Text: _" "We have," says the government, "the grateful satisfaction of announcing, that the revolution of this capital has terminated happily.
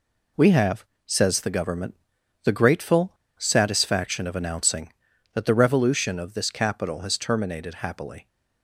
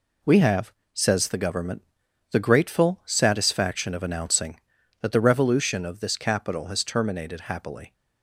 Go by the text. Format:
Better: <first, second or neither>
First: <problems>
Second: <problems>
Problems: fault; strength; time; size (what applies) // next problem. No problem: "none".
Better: second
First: pauses between "grateful" and "satisfaction"; slight; at 3.1 s; 0.26 s long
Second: none